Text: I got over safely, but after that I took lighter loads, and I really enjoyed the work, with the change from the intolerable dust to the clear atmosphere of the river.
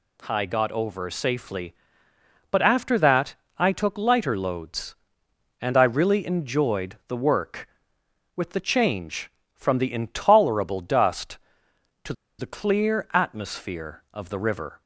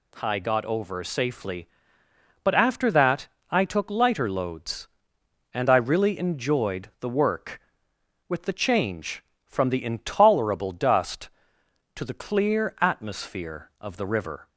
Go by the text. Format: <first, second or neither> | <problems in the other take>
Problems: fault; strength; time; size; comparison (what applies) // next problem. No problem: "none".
second | pauses between "that" and "I"; slight; at 3.3 s; 0.22 s long; slight in the second // pauses between "to" and "the"; slight; at 12.1 s; 0.25 s long